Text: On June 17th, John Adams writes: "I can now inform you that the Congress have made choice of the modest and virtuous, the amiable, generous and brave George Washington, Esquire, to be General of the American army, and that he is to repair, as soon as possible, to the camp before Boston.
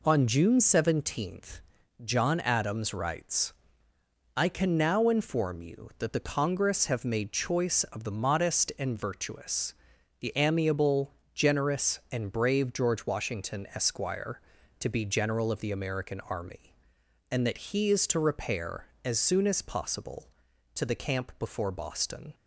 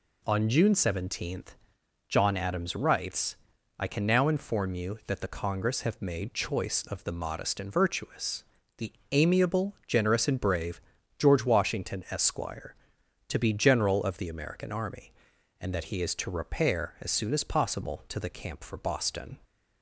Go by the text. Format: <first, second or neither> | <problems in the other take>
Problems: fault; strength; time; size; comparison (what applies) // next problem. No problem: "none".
first | pauses between "the" and "amiable"; slight; at 8.9 s; 0.18 s long // pauses between "brave" and "George"; at 10.7 s; 0.38 s long // says "for" for "before"; at 18.6 s